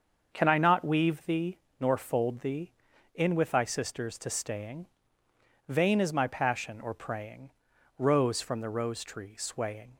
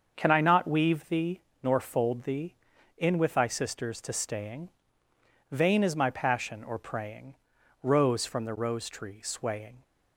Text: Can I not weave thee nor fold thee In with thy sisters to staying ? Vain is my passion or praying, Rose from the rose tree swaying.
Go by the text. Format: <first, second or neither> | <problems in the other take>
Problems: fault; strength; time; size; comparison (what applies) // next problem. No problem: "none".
neither | starts louder than the rest; the same in both // pauses between "thee" and "nor"; slight; the same in both